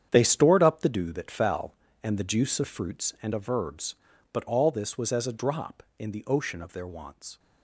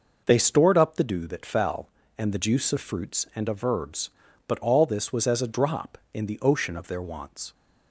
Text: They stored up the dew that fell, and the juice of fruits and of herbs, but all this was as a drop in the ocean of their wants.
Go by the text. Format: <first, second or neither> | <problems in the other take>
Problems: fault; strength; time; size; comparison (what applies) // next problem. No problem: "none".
second | gets quieter; strong; throughout; 11.5 dB